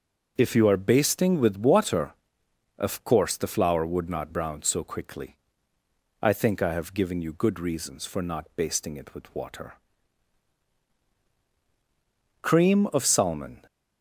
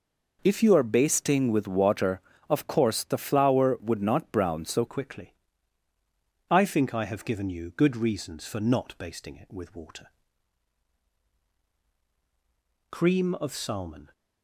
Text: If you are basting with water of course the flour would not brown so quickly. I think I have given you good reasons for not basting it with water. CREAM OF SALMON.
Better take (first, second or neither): first